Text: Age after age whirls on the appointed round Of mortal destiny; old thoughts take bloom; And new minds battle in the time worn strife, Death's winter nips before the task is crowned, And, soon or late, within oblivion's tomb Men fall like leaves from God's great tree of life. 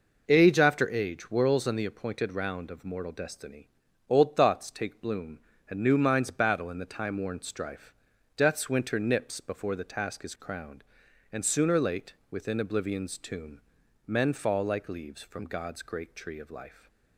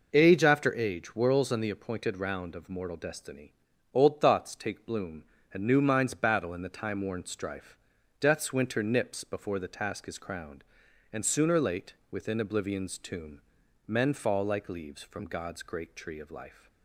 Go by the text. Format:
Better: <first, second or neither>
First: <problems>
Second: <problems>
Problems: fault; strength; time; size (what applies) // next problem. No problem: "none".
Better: neither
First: pauses between "tomb" and "Men"; noticeable; at 13.6 s; 0.46 s long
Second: pauses between "tomb" and "Men"; noticeable; at 13.4 s; 0.46 s long